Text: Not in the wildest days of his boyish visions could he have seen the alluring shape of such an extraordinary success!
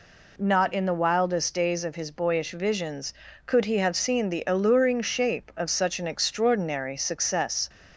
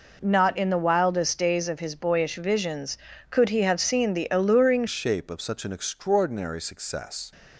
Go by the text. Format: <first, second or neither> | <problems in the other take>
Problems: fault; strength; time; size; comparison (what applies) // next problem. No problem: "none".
first | changes voice at "shape"; from 4.8 s on; 2.5 s long